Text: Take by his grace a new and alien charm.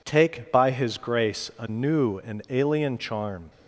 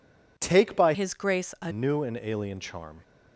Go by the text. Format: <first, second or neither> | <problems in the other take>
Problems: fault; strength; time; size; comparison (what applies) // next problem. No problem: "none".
first | changes voice from "his" to "a"; from 0.9 to 1.7 s; 0.8 s long